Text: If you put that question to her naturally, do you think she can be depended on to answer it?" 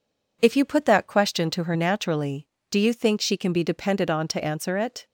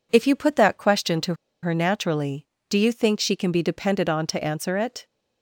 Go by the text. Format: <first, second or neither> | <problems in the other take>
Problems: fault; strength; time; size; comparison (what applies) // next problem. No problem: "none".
first | pauses between "to" and "her"; slight; at 1.3 s; 0.27 s long